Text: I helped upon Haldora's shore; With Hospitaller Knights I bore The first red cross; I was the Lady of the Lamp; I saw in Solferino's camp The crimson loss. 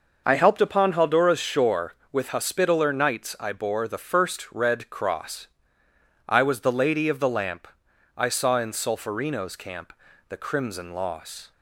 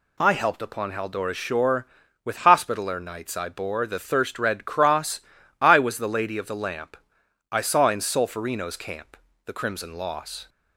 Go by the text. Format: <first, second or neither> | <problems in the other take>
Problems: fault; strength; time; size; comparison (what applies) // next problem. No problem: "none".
first | says "thirst" for "first"; at 4.0 s // pauses between "camp" and "The"; slight; at 9.1 s; 0.30 s long; slight in the first